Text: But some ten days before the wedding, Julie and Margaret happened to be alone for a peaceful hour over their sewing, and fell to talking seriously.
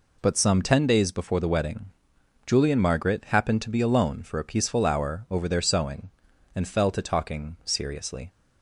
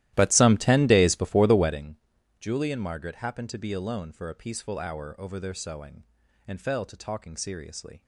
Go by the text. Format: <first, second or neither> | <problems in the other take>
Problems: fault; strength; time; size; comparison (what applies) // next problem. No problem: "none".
first | starts louder than the rest; strong; until 1.8 s; 14.5 dB